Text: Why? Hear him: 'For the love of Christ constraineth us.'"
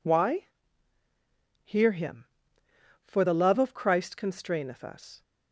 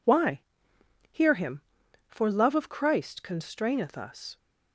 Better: first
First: none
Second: skips "the"; at 2.3 s

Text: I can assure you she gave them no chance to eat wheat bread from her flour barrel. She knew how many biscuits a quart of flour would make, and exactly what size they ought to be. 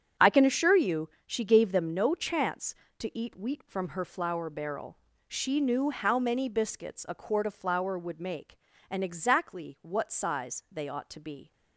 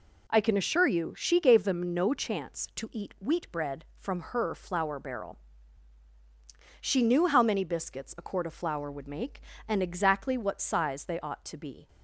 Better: second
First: starts louder than the rest; strong; until 1.3 s; 8 dB // pauses between "you" and "she"; slight; at 1.0 s; 0.18 s long // skips "bread"; at 3.6 s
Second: none

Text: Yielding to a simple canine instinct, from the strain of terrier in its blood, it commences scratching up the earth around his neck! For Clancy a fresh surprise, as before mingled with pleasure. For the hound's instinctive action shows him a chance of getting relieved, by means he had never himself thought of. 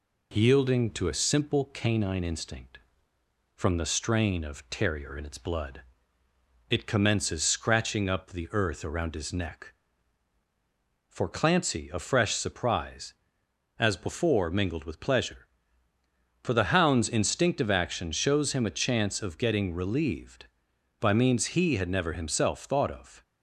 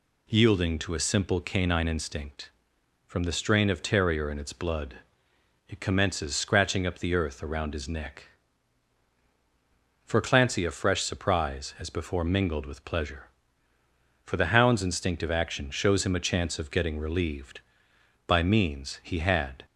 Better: first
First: none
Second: stops before "never himself thought of"; at 19.6 s

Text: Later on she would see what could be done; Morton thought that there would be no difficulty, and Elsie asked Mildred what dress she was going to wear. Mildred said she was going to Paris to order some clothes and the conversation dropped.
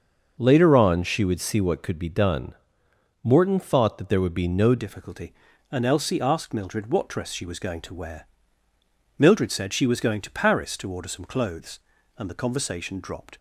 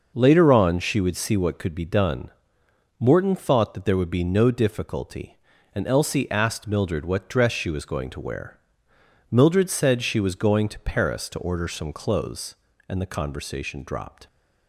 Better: second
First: starts louder than the rest; until 1.3 s; 6 dB // changes voice at "difficulty"; from 4.7 s on; 8.6 s long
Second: none

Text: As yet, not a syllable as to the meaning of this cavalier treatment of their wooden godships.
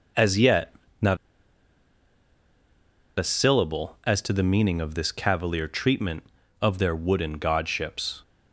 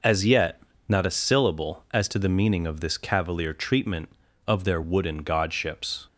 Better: second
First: pauses between "not" and "a"; strong; at 1.1 s; 2.0 s long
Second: none

